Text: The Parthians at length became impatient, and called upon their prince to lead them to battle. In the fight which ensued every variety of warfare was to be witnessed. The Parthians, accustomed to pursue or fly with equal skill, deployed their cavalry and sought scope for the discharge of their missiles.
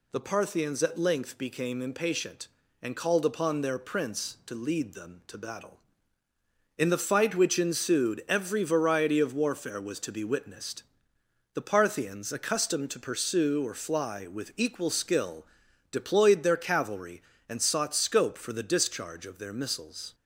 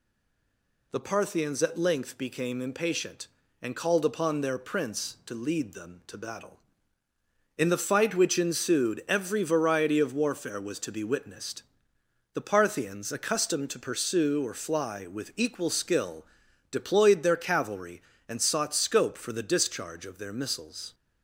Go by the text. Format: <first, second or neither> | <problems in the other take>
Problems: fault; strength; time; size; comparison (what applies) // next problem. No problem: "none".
first | stays silent before the first word; slight; until 0.9 s; 0.9 s long